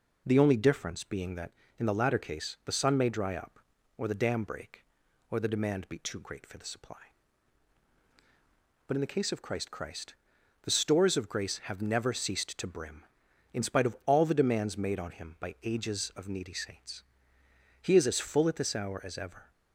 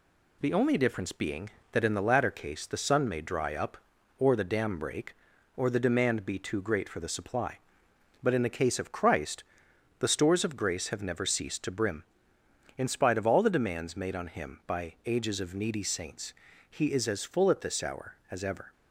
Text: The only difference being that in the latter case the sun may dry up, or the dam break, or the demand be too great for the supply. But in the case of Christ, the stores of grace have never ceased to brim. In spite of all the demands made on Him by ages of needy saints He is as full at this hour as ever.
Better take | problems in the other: second | says "Christ" twice; at 9.6 s // pauses between "saints" and "He"; noticeable; at 17.0 s; 0.78 s long; also in the second

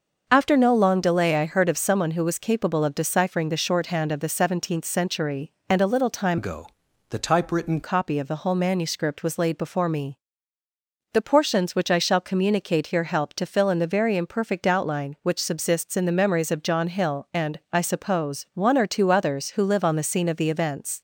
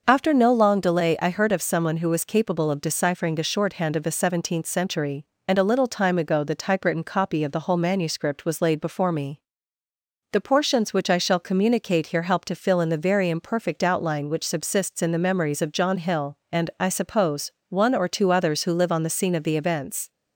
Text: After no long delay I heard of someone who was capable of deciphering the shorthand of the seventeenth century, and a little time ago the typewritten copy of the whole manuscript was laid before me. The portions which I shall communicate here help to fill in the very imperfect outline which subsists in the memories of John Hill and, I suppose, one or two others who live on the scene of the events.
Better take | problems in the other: second | starts louder than the rest; until 1.2 s; 6 dB; noticeable in the second // changes voice from "ago" to "typewritten"; from 6.3 to 7.8 s; 1.5 s long // pauses between "ago" and "the"; at 6.6 s; 0.42 s long

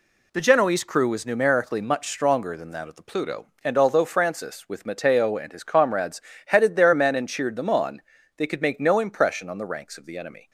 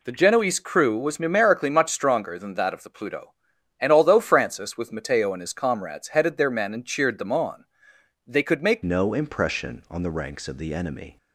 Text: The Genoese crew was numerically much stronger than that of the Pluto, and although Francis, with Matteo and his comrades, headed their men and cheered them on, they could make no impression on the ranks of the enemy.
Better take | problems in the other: first | changes voice at "no"; from 8.8 s on; 2.3 s long

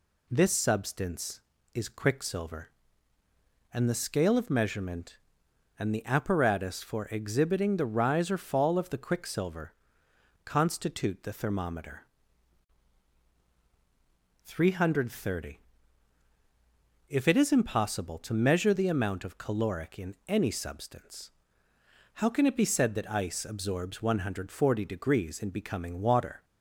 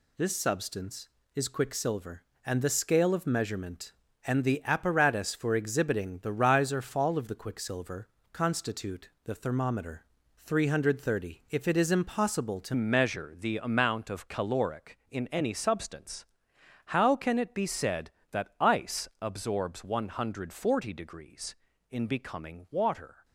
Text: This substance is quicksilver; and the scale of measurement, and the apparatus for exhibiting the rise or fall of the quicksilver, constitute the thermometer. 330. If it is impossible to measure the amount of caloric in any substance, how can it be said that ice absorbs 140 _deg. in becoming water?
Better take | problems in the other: first | pauses between "constitute" and "the"; slight; at 9.0 s; 0.16 s long // changes voice at "measure"; from 12.7 s on; 10.5 s long

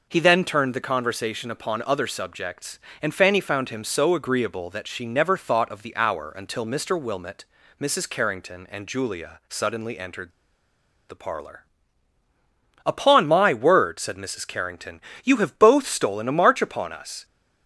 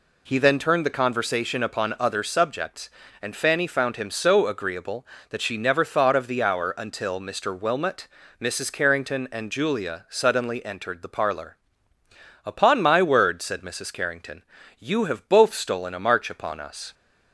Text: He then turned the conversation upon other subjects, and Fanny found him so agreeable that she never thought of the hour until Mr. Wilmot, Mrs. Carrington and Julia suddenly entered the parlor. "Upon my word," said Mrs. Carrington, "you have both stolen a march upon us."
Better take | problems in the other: second | pauses between "entered" and "the"; noticeable; at 10.3 s; 0.77 s long

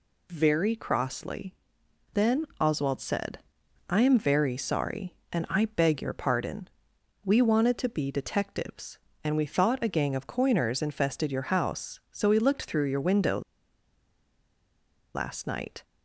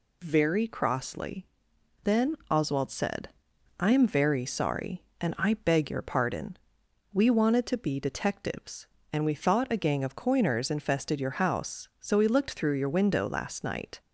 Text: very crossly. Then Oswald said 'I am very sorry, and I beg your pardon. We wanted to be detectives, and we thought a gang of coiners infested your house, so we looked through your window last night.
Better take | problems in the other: second | pauses between "Then" and "Oswald"; slight; at 2.4 s; 0.16 s long; slight in the second // pauses between "said" and "I"; noticeable; at 3.3 s; 0.50 s long; noticeable in the second // pauses between "window" and "last"; strong; at 13.4 s; 1.7 s long

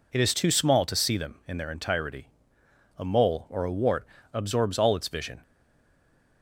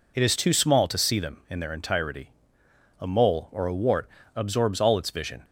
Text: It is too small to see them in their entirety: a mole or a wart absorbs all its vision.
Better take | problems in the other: second | pauses between "wart" and "absorbs"; slight; at 4.0 s; 0.26 s long; slight in the second // stays silent after the last word; from 5.4 s on; 1.0 s long

